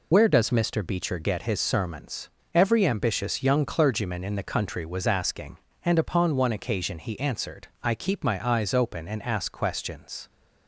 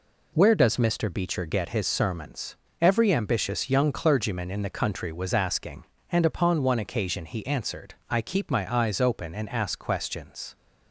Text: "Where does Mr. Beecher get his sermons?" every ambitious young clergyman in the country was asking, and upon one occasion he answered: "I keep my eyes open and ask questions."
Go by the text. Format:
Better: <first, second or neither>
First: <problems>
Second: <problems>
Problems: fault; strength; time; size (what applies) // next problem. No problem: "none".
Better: second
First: loses the start of "Where"; at 0.1 s; 45 ms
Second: none